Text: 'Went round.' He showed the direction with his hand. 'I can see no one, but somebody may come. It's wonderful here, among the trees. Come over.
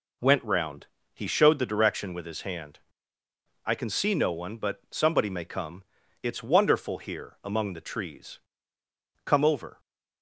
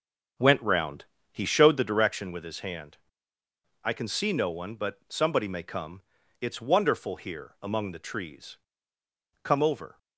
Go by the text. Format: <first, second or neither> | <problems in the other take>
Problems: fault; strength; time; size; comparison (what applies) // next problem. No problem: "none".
first | starts louder than the rest; until 2.1 s; 7 dB